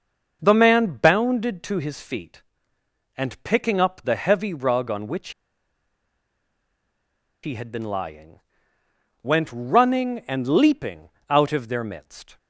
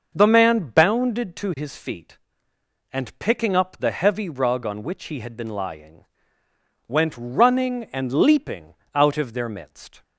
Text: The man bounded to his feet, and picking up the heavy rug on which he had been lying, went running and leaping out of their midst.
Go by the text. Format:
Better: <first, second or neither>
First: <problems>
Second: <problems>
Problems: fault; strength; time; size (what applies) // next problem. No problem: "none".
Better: second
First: starts louder than the rest; until 1.4 s; 6.5 dB // pauses between "which" and "he"; strong; at 5.3 s; 2.1 s long // pauses between "leaping" and "out"; slight; at 11.0 s; 0.20 s long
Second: starts louder than the rest; until 1.2 s; 6.5 dB // pauses between "leaping" and "out"; slight; at 8.7 s; 0.20 s long